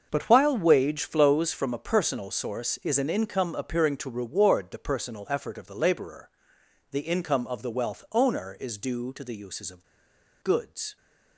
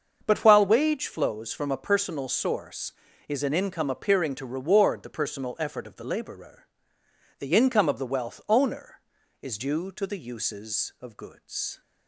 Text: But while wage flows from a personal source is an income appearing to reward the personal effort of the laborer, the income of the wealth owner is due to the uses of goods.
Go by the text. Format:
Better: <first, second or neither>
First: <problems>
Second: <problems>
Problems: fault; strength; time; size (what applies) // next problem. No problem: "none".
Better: second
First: starts louder than the rest; until 1.1 s; 6.5 dB // pauses between "of" and "goods"; noticeable; at 9.8 s; 0.57 s long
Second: starts louder than the rest; until 1.2 s; 6.5 dB